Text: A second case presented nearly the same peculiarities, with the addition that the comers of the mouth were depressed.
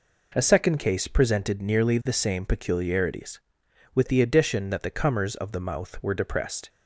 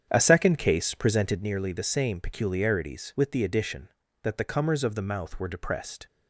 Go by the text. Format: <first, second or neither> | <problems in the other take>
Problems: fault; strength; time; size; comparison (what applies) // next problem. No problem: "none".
first | starts louder than the rest; strong; until 1.5 s; 8.5 dB